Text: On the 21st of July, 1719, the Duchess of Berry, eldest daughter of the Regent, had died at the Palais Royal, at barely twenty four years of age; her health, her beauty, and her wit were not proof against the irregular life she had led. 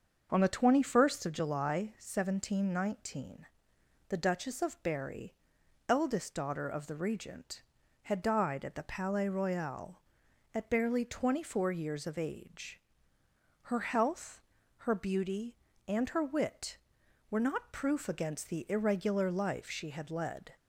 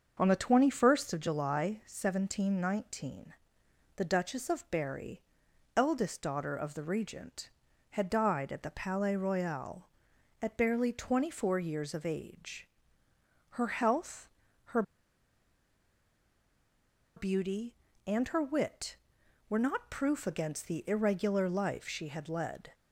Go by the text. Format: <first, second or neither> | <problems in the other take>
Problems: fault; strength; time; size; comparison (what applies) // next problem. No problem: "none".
first | starts louder than the rest; until 1.2 s; 6.5 dB; also in the first // pauses between "her" and "beauty"; strong; at 14.8 s; 2.3 s long